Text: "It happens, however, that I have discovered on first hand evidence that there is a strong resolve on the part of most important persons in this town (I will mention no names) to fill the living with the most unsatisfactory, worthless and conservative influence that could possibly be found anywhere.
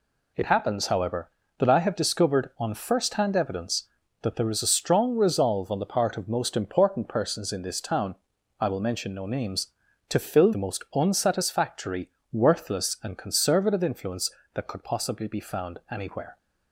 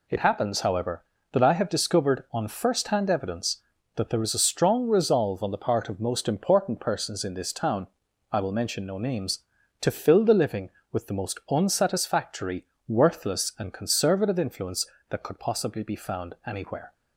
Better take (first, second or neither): second